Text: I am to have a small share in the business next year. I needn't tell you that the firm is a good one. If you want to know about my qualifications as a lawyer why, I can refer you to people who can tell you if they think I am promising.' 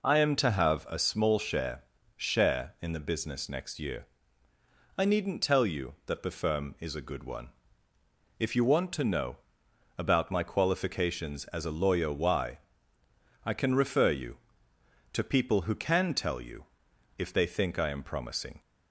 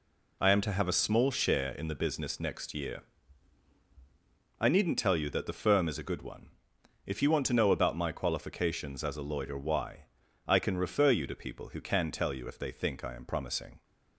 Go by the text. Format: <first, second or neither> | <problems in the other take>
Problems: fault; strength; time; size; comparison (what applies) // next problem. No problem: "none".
second | says "share" twice; at 2.1 s // pauses between "know" and "about"; noticeable; at 9.3 s; 0.62 s long // pauses between "you" and "if"; noticeable; at 16.6 s; 0.54 s long